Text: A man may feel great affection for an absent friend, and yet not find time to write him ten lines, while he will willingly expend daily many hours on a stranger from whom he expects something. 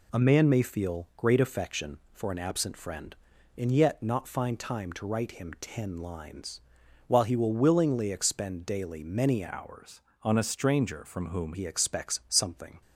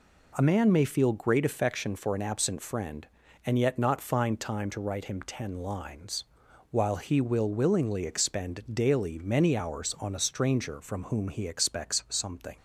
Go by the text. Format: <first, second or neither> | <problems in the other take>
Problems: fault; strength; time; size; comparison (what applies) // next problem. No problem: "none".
second | changes voice from "hours" to "whom"; from 9.4 to 11.5 s; 2.1 s long